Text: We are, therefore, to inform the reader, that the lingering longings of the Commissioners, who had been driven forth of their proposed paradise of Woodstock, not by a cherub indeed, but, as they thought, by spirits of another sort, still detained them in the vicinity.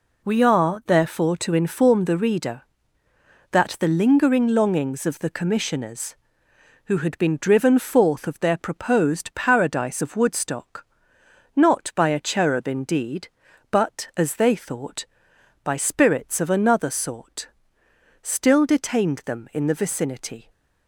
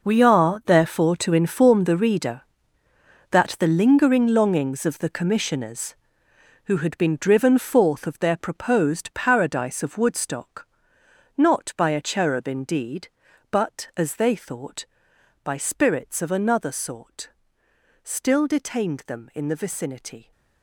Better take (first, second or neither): first